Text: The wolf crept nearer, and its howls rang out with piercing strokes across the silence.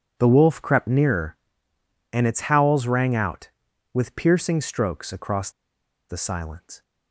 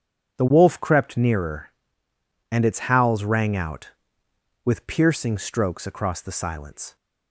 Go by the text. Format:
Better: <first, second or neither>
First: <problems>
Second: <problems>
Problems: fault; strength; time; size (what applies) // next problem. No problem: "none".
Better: second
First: pauses between "across" and "the"; noticeable; at 5.5 s; 0.58 s long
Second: none